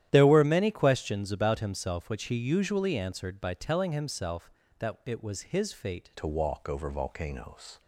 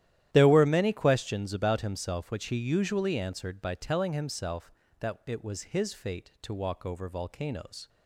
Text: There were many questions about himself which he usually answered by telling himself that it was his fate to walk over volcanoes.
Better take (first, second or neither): second